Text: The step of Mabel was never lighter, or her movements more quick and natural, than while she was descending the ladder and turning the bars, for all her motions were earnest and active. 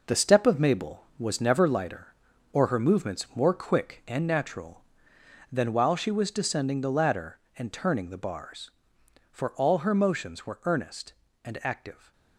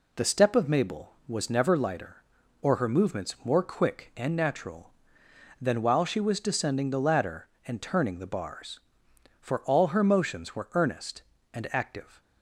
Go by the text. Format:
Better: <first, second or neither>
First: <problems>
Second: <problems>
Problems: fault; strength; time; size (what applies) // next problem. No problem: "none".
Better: second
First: gets quieter; strong; throughout; 8 dB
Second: none